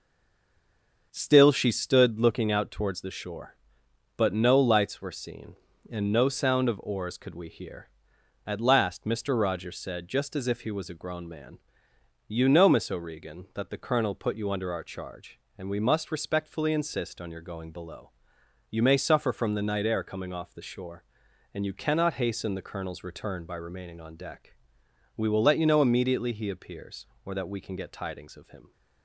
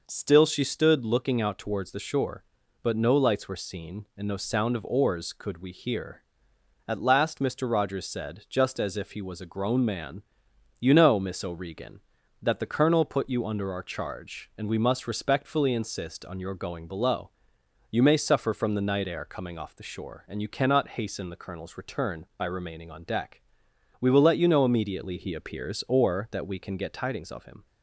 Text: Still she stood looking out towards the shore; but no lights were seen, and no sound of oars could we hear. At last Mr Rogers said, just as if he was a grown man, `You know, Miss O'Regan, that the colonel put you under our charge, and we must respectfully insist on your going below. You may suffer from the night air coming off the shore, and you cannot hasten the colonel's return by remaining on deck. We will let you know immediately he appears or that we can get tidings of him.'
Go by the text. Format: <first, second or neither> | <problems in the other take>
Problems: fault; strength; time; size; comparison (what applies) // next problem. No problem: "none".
second | stays silent before the first word; until 1.1 s; 1.1 s long // starts louder than the rest; until 2.1 s; 6.5 dB